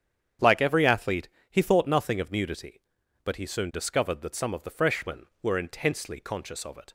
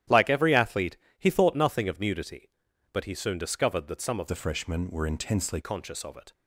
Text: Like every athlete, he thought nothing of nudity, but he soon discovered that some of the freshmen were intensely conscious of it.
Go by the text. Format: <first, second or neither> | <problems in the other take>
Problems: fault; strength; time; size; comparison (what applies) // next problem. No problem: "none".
first | starts louder than the rest; strong; until 1.3 s; 11.5 dB; strong in the first // changes voice from "the" to "intensely"; from 4.2 to 5.5 s; 1.3 s long